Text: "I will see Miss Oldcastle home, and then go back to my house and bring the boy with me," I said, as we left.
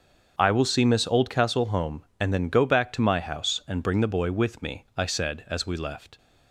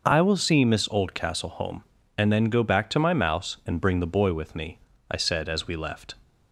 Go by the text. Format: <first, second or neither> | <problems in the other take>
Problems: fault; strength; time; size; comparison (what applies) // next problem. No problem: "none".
first | starts louder than the rest; until 1.0 s; 6.5 dB; also in the first // says "mouse" for "house"; at 3.1 s